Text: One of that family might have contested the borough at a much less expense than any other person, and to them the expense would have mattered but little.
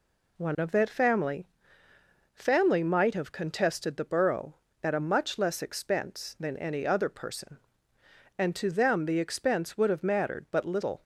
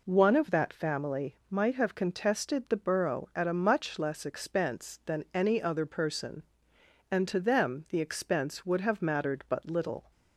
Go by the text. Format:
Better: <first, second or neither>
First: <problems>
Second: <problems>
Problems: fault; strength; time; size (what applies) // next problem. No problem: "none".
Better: second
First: says "family" twice; at 2.3 s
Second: none